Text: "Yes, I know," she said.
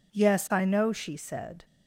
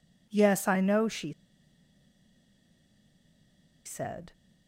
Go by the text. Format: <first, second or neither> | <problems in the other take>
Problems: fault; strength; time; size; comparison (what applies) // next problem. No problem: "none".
first | pauses between "she" and "said"; strong; at 1.3 s; 2.5 s long